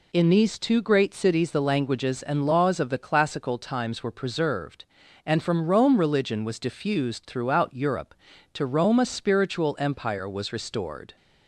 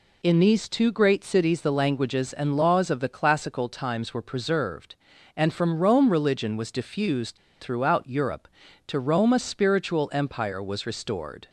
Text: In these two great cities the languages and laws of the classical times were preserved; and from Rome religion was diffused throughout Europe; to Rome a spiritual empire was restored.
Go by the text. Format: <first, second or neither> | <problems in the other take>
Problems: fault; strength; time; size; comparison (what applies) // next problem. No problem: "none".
first | pauses between "diffused" and "throughout"; slight; at 7.3 s; 0.24 s long